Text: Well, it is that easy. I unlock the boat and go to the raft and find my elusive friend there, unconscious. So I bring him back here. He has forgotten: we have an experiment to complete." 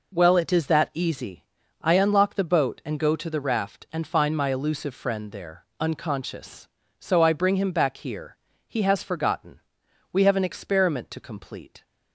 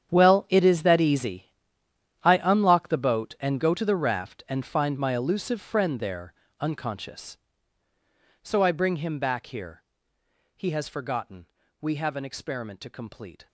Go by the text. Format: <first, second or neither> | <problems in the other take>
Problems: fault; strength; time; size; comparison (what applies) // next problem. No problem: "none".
first | gets quieter; strong; throughout; 16 dB